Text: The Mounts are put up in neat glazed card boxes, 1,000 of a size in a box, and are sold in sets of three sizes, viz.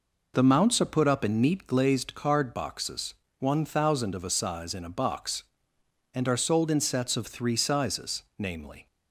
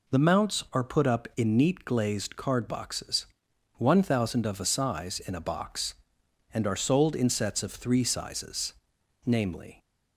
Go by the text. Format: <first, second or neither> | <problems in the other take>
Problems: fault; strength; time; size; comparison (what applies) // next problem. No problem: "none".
neither | none